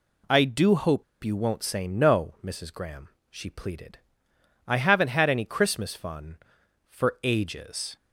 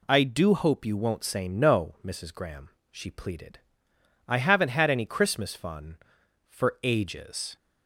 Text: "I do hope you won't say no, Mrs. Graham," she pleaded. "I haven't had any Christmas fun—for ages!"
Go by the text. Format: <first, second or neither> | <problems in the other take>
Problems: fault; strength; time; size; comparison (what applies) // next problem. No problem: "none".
second | pauses between "hope" and "you"; slight; at 1.0 s; 0.19 s long